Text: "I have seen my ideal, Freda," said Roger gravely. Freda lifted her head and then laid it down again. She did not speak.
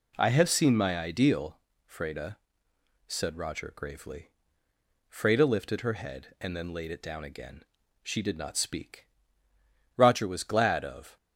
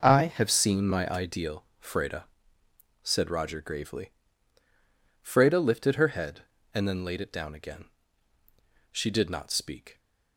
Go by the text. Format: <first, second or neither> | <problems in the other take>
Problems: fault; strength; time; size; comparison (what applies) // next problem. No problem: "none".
second | goes on to say "Roger was glad of"; noticeable; from 9.9 s on; 1.2 s long